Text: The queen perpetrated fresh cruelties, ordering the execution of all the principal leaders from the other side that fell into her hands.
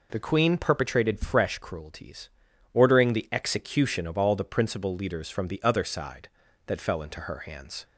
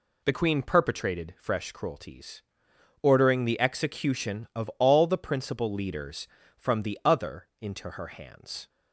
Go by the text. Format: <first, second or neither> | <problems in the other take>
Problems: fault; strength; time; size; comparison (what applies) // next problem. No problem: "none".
first | skips "side that fell"; at 7.5 s